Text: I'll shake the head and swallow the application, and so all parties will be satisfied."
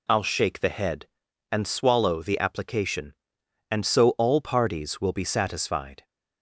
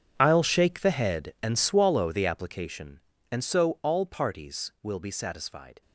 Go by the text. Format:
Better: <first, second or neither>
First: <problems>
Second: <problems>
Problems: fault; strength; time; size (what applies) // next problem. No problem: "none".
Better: first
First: none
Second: gets quieter; strong; throughout; 17 dB